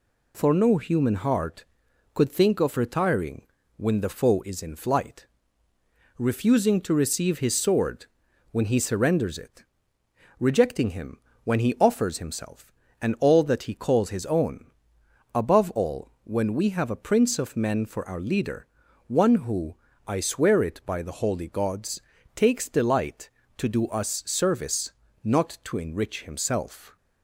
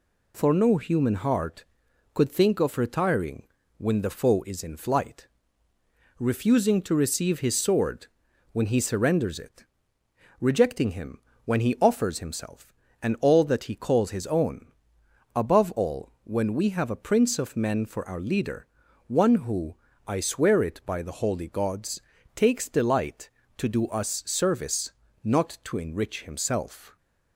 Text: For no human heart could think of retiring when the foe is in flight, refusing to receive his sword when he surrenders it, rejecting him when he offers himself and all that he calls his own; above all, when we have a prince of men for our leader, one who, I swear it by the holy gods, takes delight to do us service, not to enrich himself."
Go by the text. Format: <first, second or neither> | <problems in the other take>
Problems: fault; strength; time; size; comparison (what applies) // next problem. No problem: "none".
neither | pauses between "retiring" and "when"; slight; the same in both // pauses between "sword" and "when"; the same in both // pauses between "him" and "when"; slight; the same in both